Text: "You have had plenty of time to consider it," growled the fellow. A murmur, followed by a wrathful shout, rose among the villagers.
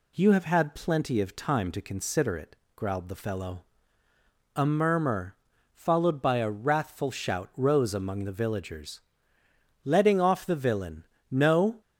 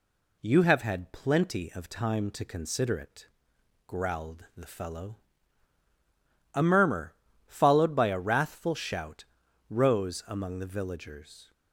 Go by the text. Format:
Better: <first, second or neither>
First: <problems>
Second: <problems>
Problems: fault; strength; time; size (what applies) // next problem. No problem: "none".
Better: second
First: goes on to say "Letting off the villain No"; strong; from 9.8 s on; 1.9 s long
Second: none